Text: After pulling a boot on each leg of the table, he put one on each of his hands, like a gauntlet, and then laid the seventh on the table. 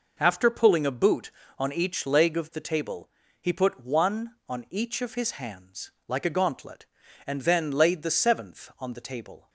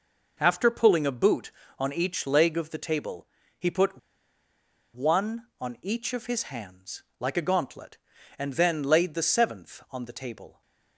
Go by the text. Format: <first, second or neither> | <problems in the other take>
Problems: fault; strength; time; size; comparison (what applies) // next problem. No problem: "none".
first | pauses between "put" and "one"; noticeable; at 3.9 s; 0.95 s long